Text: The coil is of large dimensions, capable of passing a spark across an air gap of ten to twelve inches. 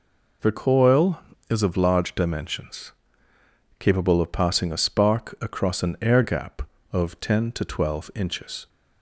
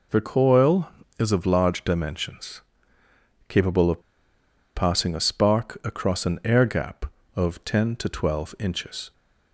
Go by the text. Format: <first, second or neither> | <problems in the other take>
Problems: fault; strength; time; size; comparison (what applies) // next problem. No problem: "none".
first | pauses between "of" and "passing"; noticeable; at 4.0 s; 0.75 s long